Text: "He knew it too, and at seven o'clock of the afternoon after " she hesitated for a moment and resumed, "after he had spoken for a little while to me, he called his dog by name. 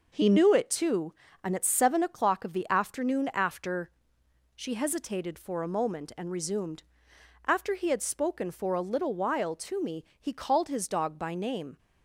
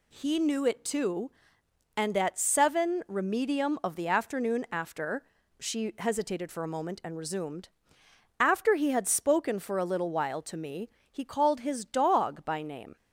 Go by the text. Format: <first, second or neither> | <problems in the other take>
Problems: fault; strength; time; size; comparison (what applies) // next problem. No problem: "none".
first | says "remedium" for "o'clock"; at 3.0 s